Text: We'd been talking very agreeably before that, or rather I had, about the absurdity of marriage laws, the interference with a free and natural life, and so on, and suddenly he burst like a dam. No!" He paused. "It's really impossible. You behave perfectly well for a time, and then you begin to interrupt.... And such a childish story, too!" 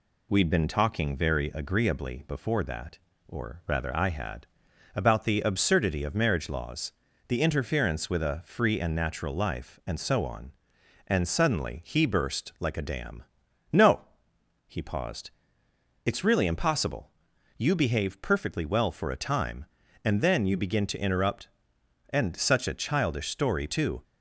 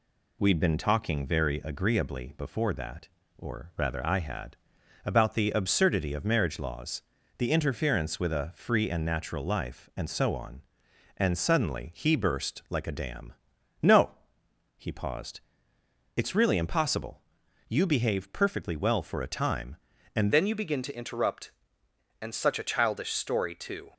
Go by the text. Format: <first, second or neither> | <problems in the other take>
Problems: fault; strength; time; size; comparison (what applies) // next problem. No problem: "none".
first | changes voice at "then"; from 20.3 s on; 3.6 s long